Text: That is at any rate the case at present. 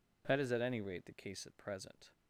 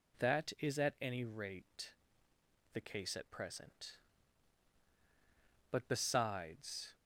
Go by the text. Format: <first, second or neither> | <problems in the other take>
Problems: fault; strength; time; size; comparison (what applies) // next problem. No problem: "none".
first | pauses between "rate" and "the"; noticeable; at 1.9 s; 0.82 s long // goes on to say "But besides"; noticeable; from 5.7 s on; 1.2 s long